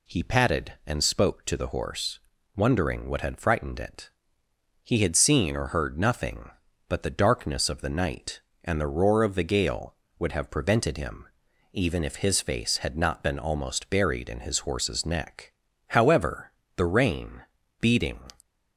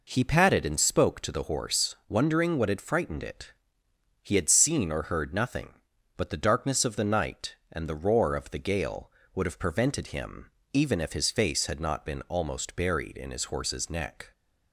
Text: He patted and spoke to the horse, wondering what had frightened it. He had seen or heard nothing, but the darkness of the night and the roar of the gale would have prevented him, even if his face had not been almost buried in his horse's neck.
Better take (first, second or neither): second